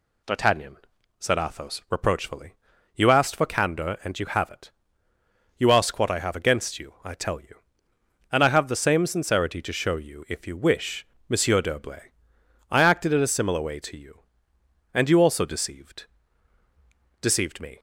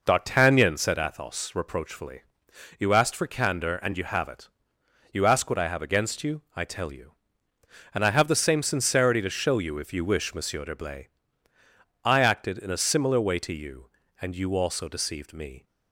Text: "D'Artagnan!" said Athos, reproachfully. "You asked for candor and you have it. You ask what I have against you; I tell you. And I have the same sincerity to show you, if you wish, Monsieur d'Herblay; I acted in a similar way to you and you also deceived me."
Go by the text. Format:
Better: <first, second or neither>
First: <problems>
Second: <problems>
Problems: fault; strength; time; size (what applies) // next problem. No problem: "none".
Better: second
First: says "deceived" twice; at 17.2 s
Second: none